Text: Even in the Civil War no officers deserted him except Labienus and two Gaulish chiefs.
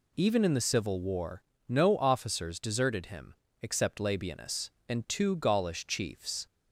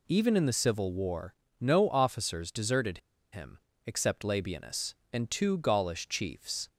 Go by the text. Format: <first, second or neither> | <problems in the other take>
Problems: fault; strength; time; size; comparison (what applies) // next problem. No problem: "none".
first | pauses between "War" and "no"; slight; at 1.3 s; 0.28 s long; slight in the first // pauses between "deserted" and "him"; slight; at 2.9 s; 0.35 s long // pauses between "him" and "except"; slight; at 3.5 s; 0.28 s long; slight in the first